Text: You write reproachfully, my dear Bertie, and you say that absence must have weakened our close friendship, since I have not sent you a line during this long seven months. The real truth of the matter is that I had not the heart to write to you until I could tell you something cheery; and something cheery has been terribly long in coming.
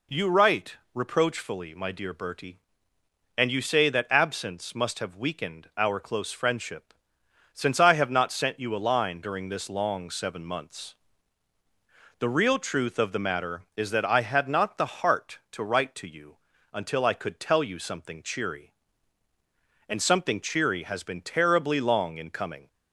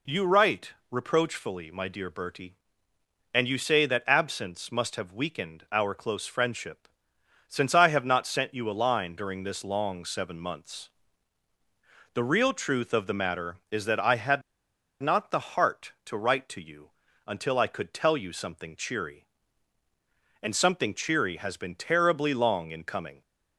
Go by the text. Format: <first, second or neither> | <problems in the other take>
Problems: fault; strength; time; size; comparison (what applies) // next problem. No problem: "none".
first | pauses between "had" and "not"; noticeable; at 14.4 s; 0.61 s long // pauses between "you" and "until"; at 16.8 s; 0.38 s long; also in the first